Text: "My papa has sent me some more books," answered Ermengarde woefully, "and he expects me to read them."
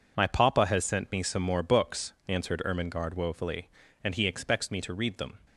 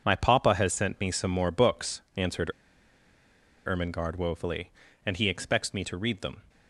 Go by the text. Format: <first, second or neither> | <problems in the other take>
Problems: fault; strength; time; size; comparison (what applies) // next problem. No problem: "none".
first | pauses between "answered" and "Ermengarde"; at 2.5 s; 1.1 s long